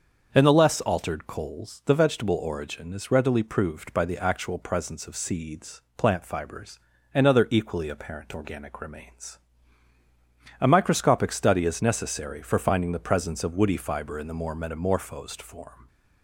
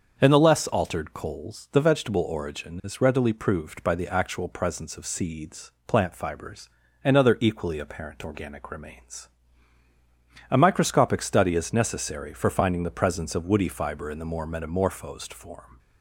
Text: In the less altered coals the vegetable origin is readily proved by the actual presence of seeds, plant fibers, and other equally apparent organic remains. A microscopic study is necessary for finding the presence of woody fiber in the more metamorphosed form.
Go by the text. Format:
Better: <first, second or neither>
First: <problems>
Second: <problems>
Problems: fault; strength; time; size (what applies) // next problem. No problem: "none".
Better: neither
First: starts louder than the rest; until 1.3 s; 6.5 dB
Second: starts louder than the rest; until 1.2 s; 6.5 dB